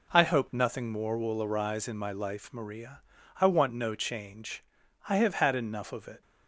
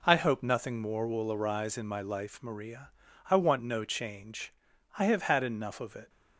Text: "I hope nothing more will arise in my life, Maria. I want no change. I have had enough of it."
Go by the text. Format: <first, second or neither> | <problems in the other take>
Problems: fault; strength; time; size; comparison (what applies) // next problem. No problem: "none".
neither | none